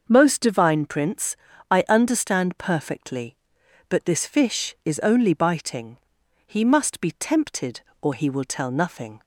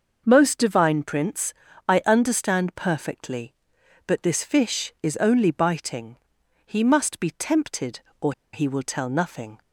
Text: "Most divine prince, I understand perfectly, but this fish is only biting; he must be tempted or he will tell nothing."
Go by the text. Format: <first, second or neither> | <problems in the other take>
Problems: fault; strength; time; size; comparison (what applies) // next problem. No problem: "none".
first | starts louder than the rest; noticeable; until 1.2 s; 6 dB; noticeable in the first // pauses between "or" and "he"; slight; at 8.3 s; 0.22 s long